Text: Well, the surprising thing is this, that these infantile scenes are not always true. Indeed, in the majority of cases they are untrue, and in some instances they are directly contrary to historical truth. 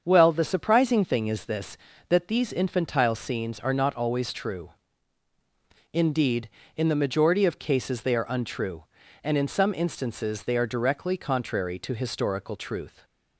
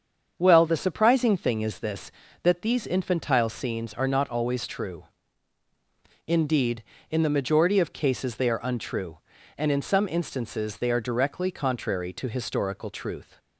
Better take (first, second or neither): neither